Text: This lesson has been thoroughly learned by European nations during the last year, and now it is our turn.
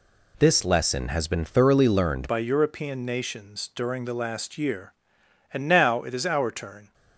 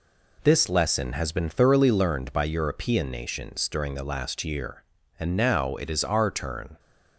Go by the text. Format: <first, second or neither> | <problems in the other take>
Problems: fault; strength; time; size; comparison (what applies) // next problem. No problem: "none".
second | changes voice at "by"; from 2.2 s on; 4.7 s long